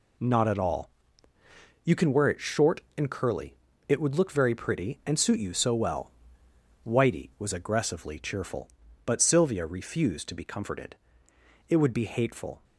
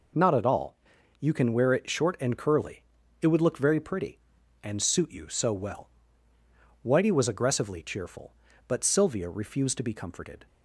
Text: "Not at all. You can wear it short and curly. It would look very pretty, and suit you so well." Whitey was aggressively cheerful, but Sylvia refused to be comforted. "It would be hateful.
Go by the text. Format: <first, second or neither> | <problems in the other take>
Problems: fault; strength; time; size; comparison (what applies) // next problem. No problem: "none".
first | stops before "It would be hateful"; at 10.4 s